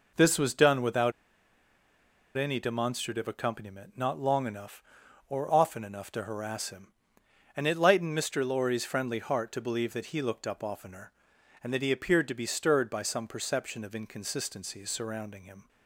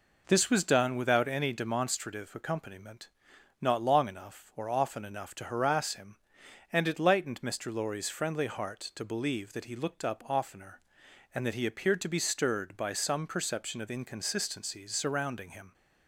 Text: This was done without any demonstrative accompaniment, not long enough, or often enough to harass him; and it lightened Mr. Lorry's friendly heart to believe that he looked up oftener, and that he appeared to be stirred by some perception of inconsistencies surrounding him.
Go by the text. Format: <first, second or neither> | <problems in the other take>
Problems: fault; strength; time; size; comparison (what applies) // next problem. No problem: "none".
second | pauses between "without" and "any"; strong; at 1.1 s; 1.2 s long